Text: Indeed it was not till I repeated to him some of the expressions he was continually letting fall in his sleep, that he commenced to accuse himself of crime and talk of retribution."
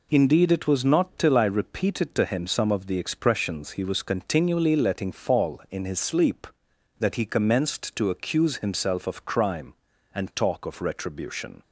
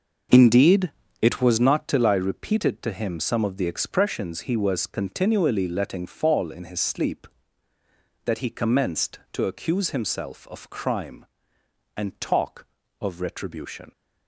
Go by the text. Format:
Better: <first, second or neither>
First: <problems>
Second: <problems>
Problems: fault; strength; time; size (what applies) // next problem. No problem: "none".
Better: first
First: none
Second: starts louder than the rest; noticeable; until 1.7 s; 6 dB // pauses between "Indeed" and "it"; slight; at 0.9 s; 0.28 s long